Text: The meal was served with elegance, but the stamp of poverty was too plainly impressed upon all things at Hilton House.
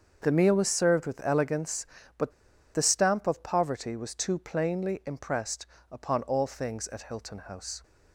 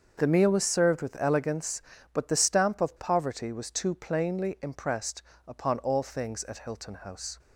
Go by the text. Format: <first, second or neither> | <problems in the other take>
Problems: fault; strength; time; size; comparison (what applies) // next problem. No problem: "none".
second | starts louder than the rest; until 1.2 s; 7 dB; also in the second // pauses between "but" and "the"; at 2.3 s; 0.42 s long // pauses between "impressed" and "upon"; slight; at 5.6 s; 0.24 s long; slight in the second